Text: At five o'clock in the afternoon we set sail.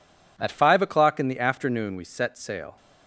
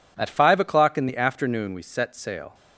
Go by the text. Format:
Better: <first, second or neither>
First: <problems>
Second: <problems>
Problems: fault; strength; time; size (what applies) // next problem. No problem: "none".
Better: neither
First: none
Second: none